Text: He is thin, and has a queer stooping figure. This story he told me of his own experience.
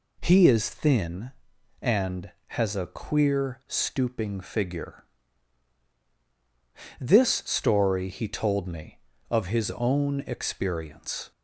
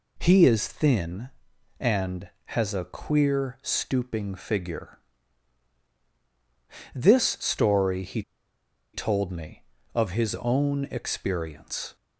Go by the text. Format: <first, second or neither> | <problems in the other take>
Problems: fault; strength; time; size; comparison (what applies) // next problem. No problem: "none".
first | pauses between "he" and "told"; noticeable; at 8.2 s; 0.72 s long